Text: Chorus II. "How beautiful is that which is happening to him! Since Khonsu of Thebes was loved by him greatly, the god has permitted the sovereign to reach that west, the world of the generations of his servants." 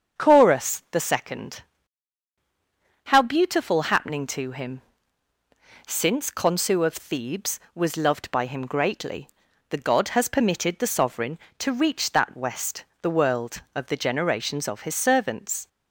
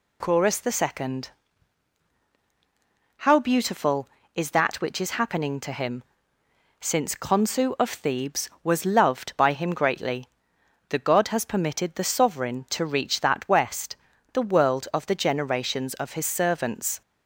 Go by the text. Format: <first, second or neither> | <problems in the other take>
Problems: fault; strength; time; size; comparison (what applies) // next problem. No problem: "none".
second | starts louder than the rest; until 1.2 s; 7 dB // skips "is that which is"; at 3.9 s